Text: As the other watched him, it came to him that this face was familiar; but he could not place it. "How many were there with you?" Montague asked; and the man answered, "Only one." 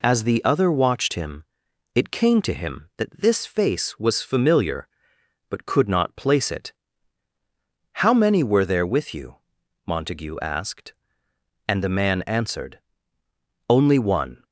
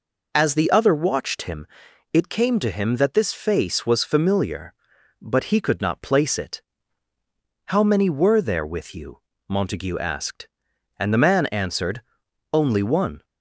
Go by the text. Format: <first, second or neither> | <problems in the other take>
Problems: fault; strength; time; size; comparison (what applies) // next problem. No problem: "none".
second | skips "he"; at 5.6 s